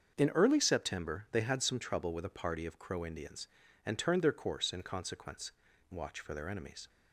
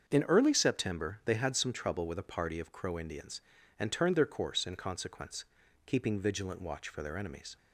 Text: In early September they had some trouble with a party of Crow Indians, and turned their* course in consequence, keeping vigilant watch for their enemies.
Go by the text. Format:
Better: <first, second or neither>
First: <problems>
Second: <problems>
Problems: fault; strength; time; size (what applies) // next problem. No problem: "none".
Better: second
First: starts louder than the rest; until 1.1 s; 7 dB // skips "keeping vigilant"; at 5.7 s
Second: starts louder than the rest; until 1.0 s; 7 dB